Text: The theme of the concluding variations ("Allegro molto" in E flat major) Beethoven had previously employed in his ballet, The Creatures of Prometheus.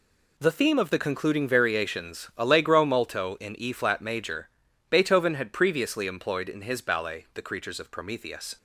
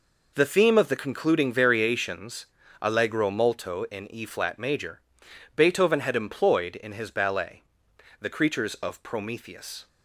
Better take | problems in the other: first | skips "previously"; at 6.1 s

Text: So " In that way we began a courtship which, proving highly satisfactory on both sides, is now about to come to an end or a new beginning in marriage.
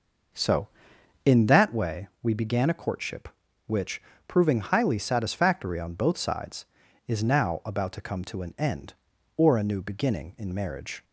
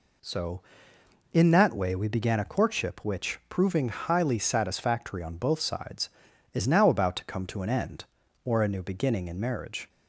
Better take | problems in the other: second | starts louder than the rest; noticeable; until 1.7 s; 5.5 dB

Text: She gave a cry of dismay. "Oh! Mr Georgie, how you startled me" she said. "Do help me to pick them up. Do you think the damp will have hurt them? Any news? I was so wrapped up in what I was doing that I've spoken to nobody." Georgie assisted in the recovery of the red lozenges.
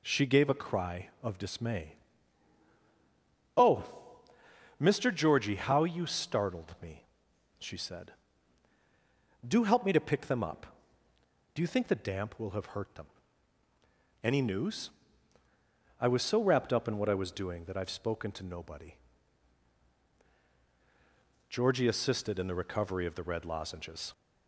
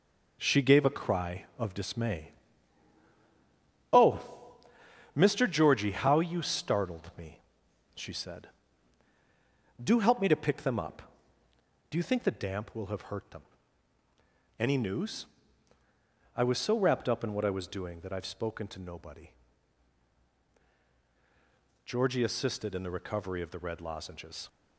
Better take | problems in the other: first | gets quieter; noticeable; throughout; 5.5 dB // pauses between "me" and "she"; noticeable; at 7.3 s; 0.54 s long; noticeable in the first

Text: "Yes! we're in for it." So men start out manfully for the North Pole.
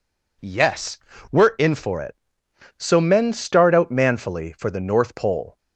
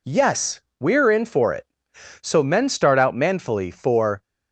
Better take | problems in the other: first | stops before "the North Pole"; at 4.2 s

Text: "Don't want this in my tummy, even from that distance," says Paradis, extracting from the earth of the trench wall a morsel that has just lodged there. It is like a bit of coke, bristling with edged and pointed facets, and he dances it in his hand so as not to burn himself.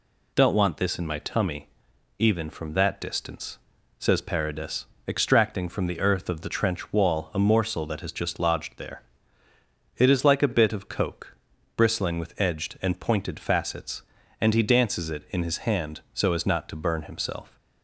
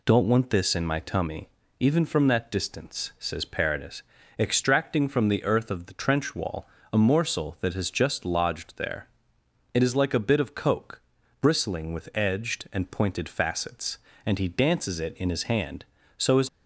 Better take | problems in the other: first | pauses between "wall" and "a"; slight; at 6.6 s; 0.26 s long // stops before "not to burn himself"; at 16.4 s

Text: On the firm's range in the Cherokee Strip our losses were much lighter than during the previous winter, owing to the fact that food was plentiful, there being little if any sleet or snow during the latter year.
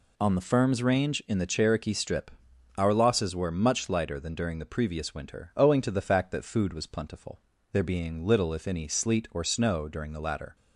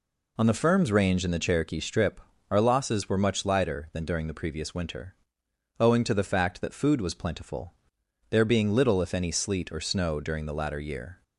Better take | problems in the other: second | pauses between "Strip" and "our"; noticeable; at 2.3 s; 0.46 s long; slight in the second // stops before "year"; at 10.5 s

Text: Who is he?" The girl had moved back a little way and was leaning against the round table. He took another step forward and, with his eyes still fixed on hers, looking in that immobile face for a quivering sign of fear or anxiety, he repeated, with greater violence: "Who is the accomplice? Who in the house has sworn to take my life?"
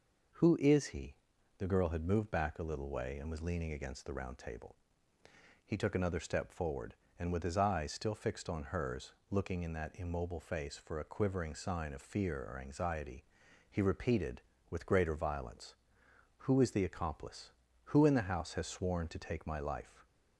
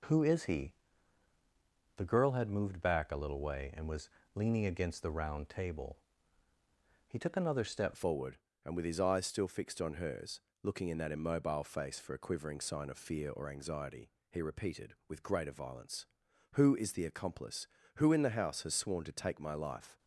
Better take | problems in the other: first | pauses between "was" and "leaning"; slight; at 4.0 s; 0.26 s long // changes voice at "forward"; from 7.9 s on; 12.0 s long

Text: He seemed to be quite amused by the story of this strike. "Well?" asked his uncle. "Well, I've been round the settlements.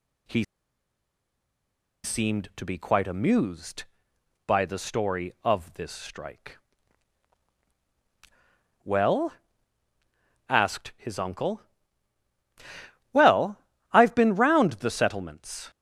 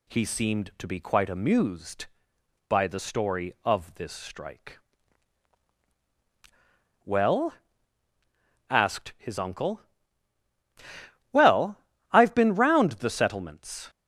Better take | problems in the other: second | pauses between "He" and "seemed"; strong; at 0.4 s; 1.6 s long

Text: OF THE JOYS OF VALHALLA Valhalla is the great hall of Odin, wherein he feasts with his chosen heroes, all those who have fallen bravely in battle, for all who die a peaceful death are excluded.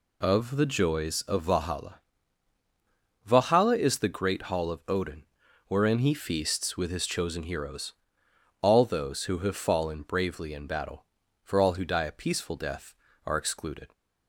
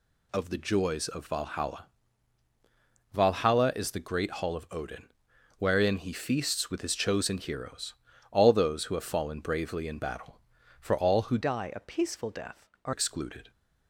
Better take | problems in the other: first | pauses between "VALHALLA" and "Valhalla"; strong; at 1.8 s; 1.3 s long; strong in the first // changes voice from "die" to "are"; from 11.4 to 12.9 s; 1.5 s long

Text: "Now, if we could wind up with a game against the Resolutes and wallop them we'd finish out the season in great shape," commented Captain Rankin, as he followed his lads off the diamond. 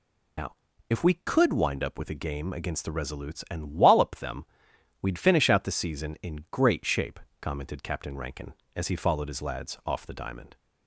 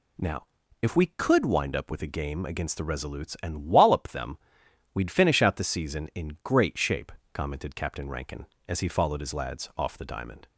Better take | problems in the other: second | loses the start of "Now"; at 0.3 s; 100 ms // pauses between "them" and "we'd"; noticeable; at 4.4 s; 0.56 s long; noticeable in the second

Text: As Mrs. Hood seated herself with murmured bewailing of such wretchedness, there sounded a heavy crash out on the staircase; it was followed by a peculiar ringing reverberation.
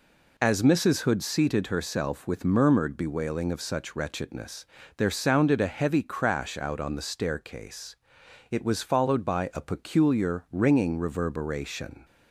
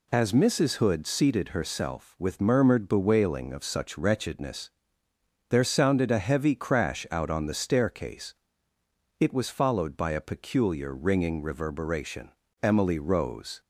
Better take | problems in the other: first | goes on to say "Emily rose"; noticeable; from 12.6 s on; 0.98 s long

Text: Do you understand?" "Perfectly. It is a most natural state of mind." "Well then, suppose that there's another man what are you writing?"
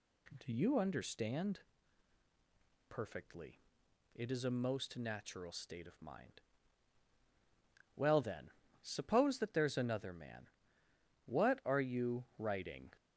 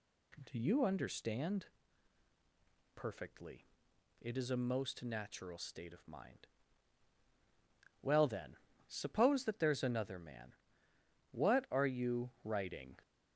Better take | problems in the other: neither | pauses between "man" and "what"; noticeable; the same in both

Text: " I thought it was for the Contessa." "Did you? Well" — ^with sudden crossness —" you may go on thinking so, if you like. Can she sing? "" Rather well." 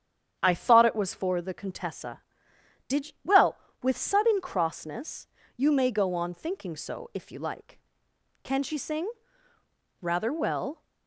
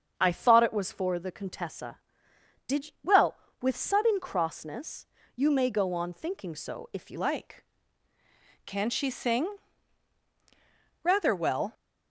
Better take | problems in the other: first | starts louder than the rest; strong; until 1.1 s; 8 dB; strong in the first // changes voice at "like"; from 7.1 s on; 4.6 s long

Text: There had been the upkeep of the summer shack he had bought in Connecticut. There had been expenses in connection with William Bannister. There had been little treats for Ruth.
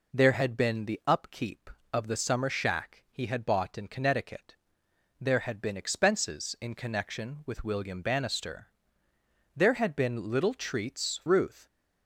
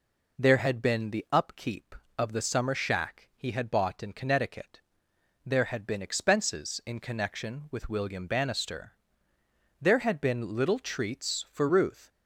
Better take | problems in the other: second | skips "for"; at 11.2 s

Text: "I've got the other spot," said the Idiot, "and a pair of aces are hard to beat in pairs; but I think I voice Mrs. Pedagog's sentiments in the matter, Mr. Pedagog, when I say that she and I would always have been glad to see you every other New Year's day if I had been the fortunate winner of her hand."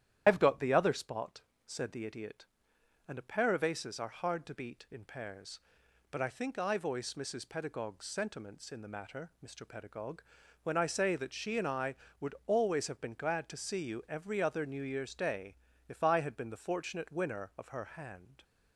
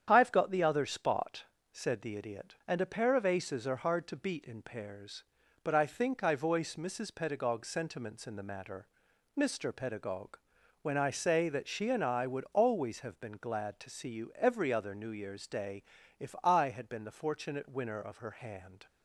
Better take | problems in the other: second | loses the start of "I've"; at 0.2 s; 105 ms // starts louder than the rest; strong; until 1.2 s; 11 dB; strong in the second // pauses between "day" and "if"; slight; at 15.5 s; 0.32 s long; slight in the second

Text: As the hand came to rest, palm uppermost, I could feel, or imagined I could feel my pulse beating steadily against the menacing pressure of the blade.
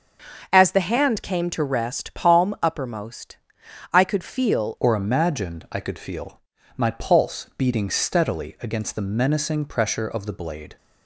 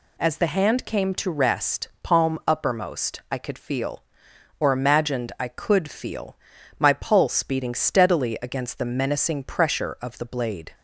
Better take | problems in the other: second | starts louder than the rest; until 1.5 s; 6.5 dB // changes voice at "or"; from 4.7 s on; 6.0 s long // pauses between "feel" and "my"; slight; at 6.4 s; 0.36 s long; also in the second

